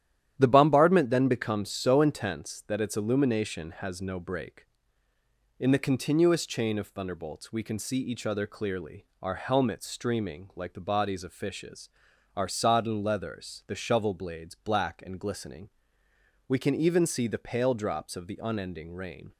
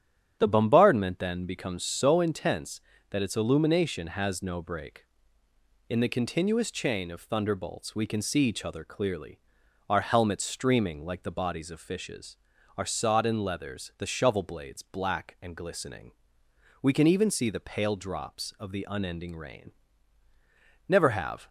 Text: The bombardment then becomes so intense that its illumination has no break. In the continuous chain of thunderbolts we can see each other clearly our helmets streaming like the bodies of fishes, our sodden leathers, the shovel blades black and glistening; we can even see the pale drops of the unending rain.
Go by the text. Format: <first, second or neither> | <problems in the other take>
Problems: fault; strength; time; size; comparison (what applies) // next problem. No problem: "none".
first | starts louder than the rest; strong; until 1.4 s; 9.5 dB; strong in the first // pauses between "clearly" and "our"; noticeable; at 9.3 s; 0.48 s long; slight in the first // goes on to say "Never have"; from 20.8 s on; 0.60 s long